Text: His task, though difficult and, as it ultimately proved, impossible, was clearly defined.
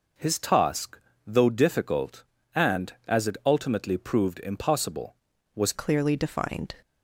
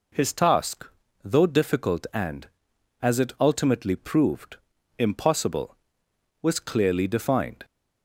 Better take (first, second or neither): second